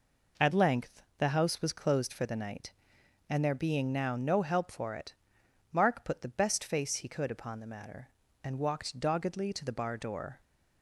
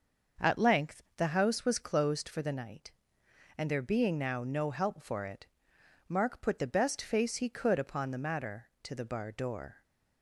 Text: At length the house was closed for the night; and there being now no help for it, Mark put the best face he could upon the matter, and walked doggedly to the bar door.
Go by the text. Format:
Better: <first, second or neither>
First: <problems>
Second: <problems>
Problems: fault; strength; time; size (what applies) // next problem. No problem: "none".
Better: first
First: none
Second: starts louder than the rest; until 1.5 s; 6.5 dB // pauses between "length" and "the"; slight; at 1.0 s; 0.16 s long // skips "and walked doggedly"; at 8.7 s